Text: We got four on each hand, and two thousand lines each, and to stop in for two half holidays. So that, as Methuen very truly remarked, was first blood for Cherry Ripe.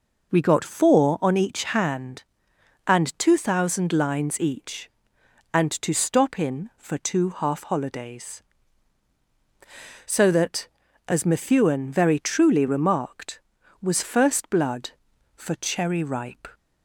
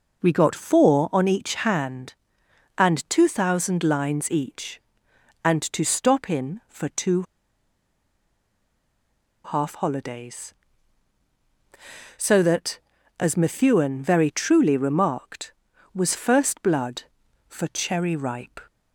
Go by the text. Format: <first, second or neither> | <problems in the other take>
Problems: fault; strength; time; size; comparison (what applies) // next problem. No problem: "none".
first | pauses between "two" and "half"; strong; at 7.2 s; 2.2 s long